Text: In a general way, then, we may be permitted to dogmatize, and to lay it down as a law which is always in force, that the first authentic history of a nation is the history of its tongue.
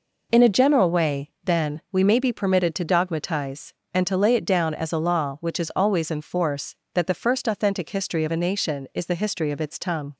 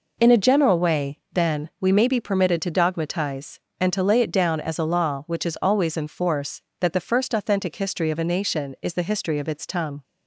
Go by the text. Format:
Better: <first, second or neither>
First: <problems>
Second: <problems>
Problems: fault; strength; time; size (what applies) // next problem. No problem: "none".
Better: neither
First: none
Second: none